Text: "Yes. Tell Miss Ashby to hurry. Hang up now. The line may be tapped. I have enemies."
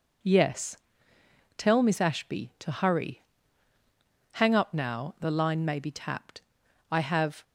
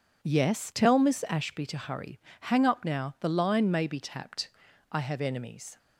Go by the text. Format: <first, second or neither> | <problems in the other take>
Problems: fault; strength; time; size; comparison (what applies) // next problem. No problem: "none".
second | stops before "enemies"; at 7.4 s